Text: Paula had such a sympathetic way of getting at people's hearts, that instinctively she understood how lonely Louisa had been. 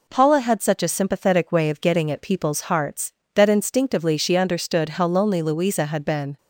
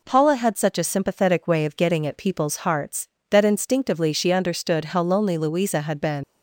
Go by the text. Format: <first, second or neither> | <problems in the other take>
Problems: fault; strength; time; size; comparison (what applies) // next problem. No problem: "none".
first | leaves "been" unfinished; at 6.2 s; 90 ms